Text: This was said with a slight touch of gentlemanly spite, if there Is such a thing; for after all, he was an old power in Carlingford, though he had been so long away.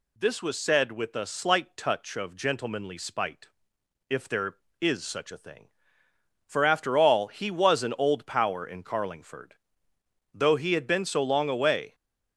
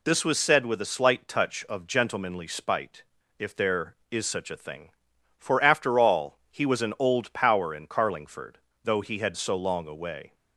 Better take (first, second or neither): first